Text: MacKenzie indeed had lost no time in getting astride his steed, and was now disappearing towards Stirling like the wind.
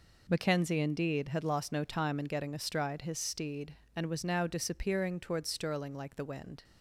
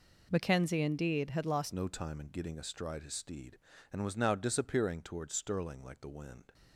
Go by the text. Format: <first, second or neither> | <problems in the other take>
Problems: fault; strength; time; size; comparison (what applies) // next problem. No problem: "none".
first | changes voice at "no"; from 1.7 s on; 4.8 s long